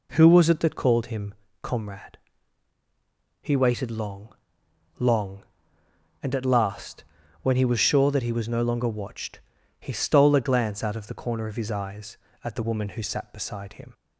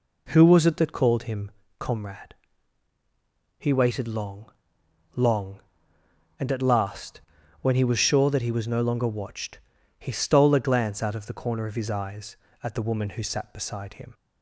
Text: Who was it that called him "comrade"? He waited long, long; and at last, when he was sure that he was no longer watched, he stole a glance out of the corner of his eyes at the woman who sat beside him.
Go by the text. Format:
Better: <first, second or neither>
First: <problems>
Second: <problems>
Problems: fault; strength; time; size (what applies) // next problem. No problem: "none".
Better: neither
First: pauses between "him" and "comrade"; slight; at 1.3 s; 0.28 s long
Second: pauses between "him" and "comrade"; slight; at 1.5 s; 0.28 s long